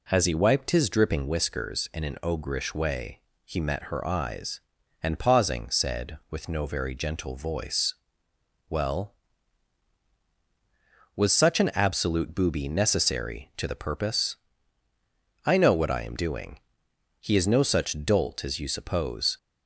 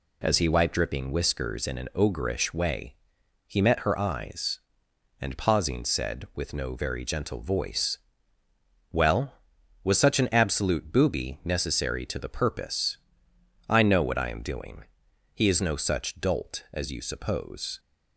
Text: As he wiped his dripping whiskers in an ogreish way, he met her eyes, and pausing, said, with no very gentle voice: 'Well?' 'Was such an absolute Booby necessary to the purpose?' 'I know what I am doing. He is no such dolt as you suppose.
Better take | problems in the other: first | skips "his"; at 0.7 s

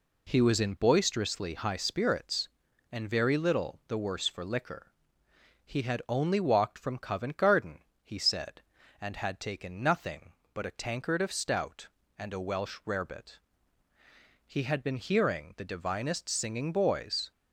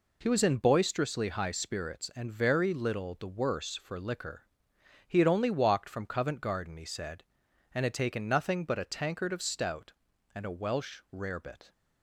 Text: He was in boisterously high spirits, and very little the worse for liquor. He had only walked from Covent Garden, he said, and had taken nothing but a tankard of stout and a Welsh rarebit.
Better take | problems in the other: second | goes on to say "He had been hearing the divinest singing boys"; strong; from 14.4 s on; 2.8 s long

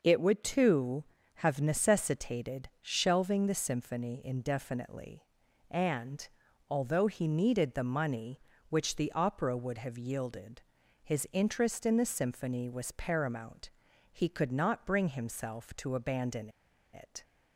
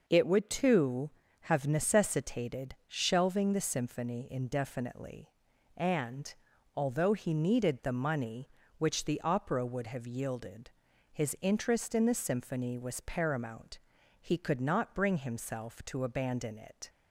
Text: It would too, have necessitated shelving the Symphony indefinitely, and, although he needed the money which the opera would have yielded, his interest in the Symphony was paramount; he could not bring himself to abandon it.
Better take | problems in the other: second | pauses between "abandon" and "it"; at 16.4 s; 0.44 s long

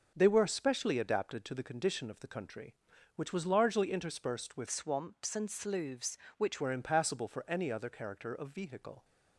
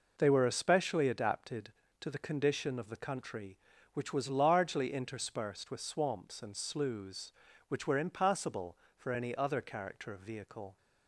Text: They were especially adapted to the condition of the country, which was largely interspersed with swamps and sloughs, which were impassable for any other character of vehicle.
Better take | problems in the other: second | changes voice from "swamps" to "which"; from 4.6 to 6.6 s; 2.0 s long

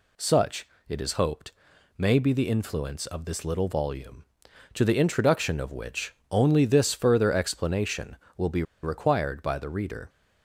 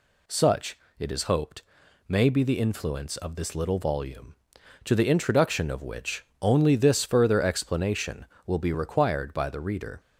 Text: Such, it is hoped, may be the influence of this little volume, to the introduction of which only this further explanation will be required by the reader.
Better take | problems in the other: second | pauses between "which" and "only"; slight; at 6.1 s; 0.16 s long; slight in the second // pauses between "be" and "required"; slight; at 8.6 s; 0.19 s long

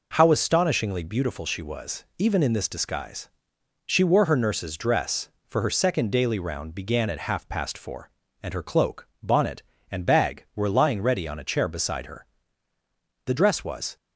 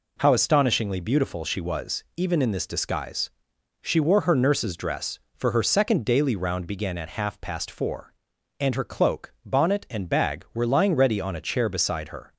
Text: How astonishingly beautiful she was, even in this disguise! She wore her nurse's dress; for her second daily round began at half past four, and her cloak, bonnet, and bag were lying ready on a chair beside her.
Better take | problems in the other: second | goes on to say "The dress was"; noticeable; from 13.2 s on; 0.72 s long

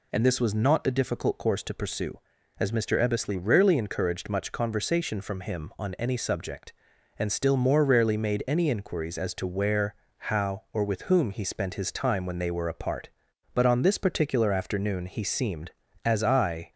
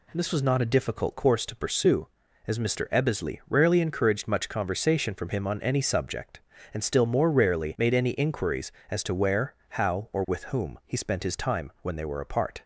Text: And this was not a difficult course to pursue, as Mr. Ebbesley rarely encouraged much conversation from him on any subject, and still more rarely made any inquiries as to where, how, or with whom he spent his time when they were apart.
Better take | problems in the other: second | goes on to say "But on this particular afternoon he seemed as I"; strong; from 13.5 s on; 3.1 s long

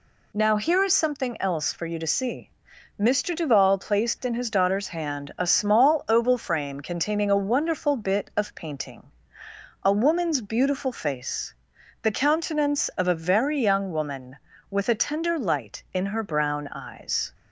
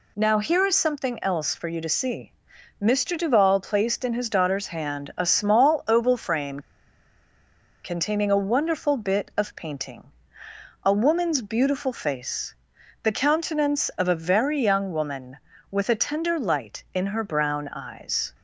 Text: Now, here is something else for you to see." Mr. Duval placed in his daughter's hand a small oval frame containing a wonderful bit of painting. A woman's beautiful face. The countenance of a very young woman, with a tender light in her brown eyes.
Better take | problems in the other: first | pauses between "frame" and "containing"; at 6.5 s; 1.2 s long

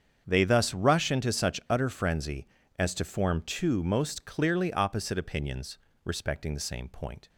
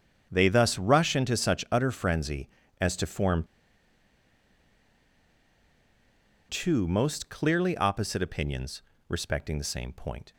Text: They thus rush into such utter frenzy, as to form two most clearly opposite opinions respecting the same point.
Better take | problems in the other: first | starts louder than the rest; strong; until 1.3 s; 7.5 dB; strong in the first // pauses between "form" and "two"; strong; at 3.4 s; 3.0 s long // pauses between "opinions" and "respecting"; slight; at 8.8 s; 0.26 s long; slight in the first

